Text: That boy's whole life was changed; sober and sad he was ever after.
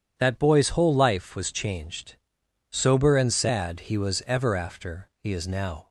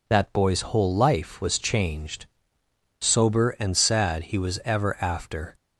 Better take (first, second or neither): second